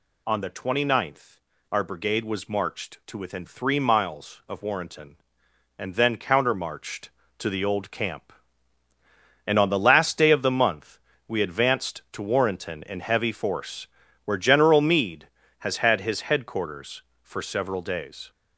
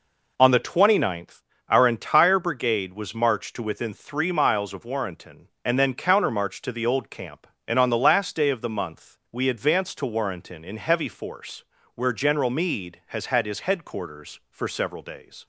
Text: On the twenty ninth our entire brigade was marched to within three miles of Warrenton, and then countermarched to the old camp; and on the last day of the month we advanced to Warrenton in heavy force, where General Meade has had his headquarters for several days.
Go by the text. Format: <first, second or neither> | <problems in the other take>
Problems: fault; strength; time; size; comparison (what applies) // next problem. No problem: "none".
second | pauses between "ninth" and "our"; slight; at 1.3 s; 0.34 s long; slight in the second // skips "entire"; at 1.8 s // pauses between "month" and "we"; slight; at 10.9 s; 0.28 s long